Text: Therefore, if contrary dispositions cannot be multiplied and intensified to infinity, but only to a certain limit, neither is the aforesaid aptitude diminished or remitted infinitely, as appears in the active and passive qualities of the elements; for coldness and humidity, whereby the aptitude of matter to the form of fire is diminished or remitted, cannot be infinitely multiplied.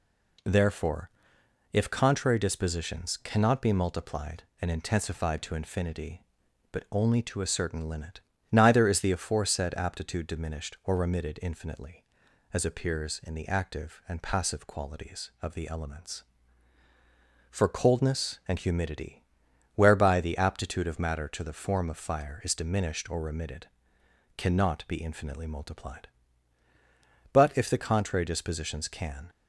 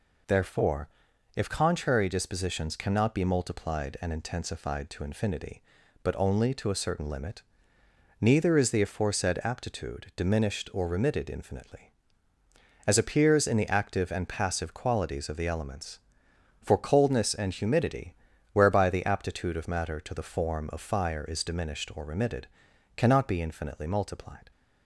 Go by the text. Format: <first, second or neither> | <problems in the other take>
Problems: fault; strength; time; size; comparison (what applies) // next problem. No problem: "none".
second | goes on to say "But if the contrary dispositions can"; strong; from 27.3 s on; 1.9 s long